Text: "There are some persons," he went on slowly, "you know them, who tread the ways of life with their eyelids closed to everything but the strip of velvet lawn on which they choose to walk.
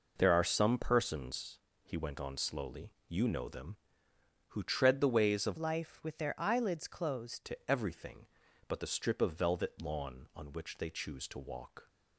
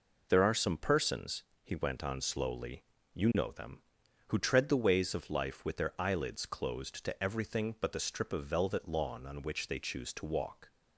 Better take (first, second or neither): second